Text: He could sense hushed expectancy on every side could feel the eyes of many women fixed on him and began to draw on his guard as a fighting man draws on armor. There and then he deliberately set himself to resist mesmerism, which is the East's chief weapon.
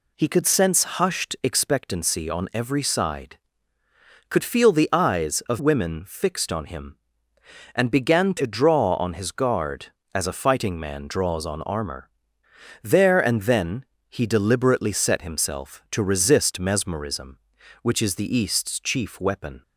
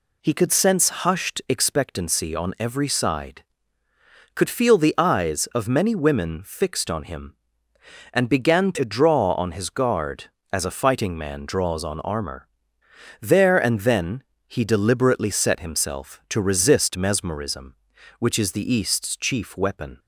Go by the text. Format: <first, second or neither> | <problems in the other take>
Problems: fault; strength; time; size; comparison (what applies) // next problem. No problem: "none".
second | skips "many"; at 5.5 s // pauses between "then" and "he"; slight; at 13.8 s; 0.24 s long; slight in the second